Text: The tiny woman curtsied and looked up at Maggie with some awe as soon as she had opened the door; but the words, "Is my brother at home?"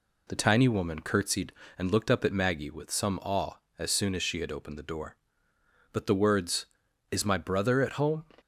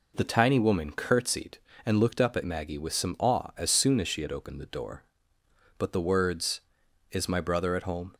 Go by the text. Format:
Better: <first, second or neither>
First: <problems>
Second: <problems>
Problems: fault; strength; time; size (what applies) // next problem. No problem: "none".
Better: neither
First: none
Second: none